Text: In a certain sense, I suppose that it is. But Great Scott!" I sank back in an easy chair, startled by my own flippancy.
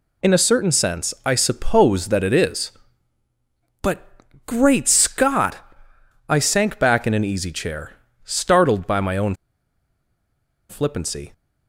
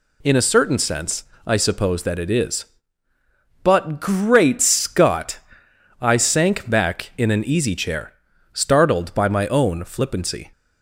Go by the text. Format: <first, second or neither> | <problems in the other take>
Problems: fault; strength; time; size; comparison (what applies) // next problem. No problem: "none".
second | pauses between "But" and "Great"; at 4.0 s; 0.42 s long // pauses between "own" and "flippancy"; strong; at 9.3 s; 1.3 s long